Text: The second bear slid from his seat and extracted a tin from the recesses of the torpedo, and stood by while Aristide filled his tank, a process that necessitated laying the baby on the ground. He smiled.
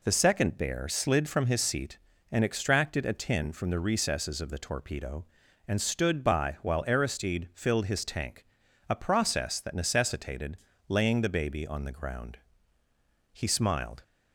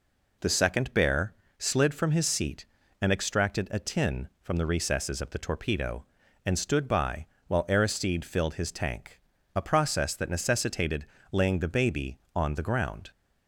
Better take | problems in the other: first | pauses between "bear" and "slid"; slight; at 1.3 s; 0.26 s long // pauses between "by" and "while"; slight; at 7.2 s; 0.22 s long // pauses between "necessitated" and "laying"; slight; at 11.0 s; 0.28 s long; slight in the first // stops before "He smiled"; at 13.1 s

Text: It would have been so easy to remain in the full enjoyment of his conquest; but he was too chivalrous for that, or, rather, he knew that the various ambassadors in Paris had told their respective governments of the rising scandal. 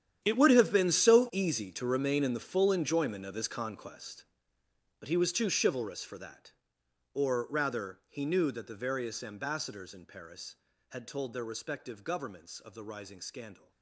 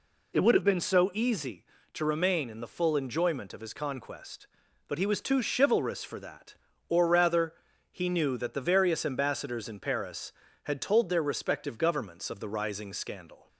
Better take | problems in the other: second | gets quieter; strong; throughout; 16.5 dB

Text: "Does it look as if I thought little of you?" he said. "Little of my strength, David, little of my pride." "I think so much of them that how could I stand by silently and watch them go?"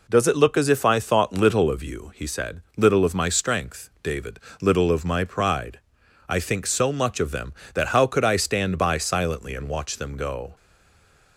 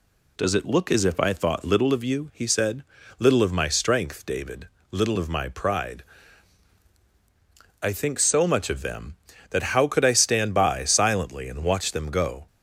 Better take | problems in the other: second | stays silent after the last word; slight; from 10.5 s on; 0.8 s long

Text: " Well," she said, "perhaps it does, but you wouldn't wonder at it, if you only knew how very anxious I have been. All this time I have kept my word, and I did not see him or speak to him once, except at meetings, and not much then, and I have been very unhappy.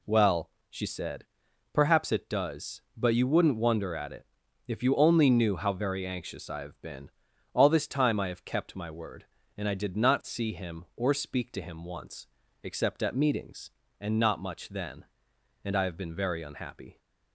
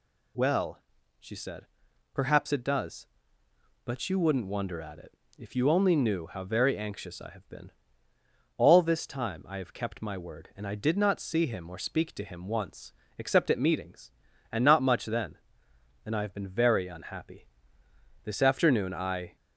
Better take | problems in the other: first | goes on to say "This afternoon I"; noticeable; from 18.2 s on; 1.1 s long

